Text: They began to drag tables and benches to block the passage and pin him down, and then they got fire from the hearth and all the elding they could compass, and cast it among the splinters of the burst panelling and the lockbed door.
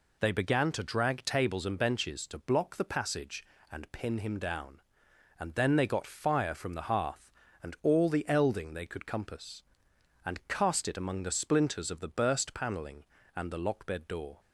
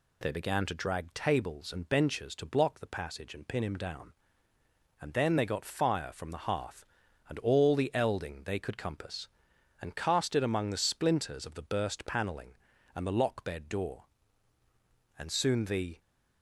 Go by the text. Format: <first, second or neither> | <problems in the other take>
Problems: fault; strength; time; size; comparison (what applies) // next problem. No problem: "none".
first | goes on to say "And soon the"; noticeable; from 15.1 s on; 0.82 s long